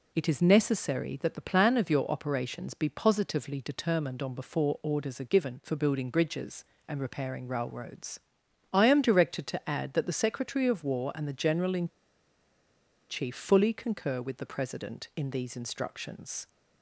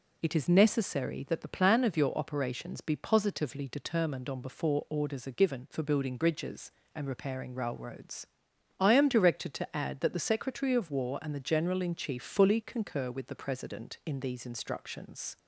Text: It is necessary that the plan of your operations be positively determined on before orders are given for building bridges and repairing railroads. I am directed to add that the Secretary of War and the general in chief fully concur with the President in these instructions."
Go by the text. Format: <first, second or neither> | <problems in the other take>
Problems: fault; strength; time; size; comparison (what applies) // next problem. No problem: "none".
second | pauses between "in" and "chief"; at 11.8 s; 1.2 s long